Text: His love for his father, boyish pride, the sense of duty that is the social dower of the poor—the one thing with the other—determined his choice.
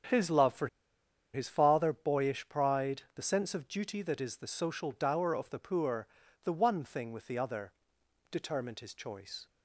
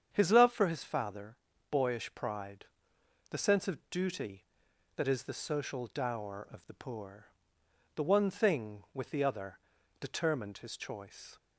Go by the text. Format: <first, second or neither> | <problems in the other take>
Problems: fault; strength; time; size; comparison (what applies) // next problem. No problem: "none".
second | starts louder than the rest; strong; until 1.7 s; 8.5 dB; strong in the second // pauses between "for" and "his"; noticeable; at 0.6 s; 0.66 s long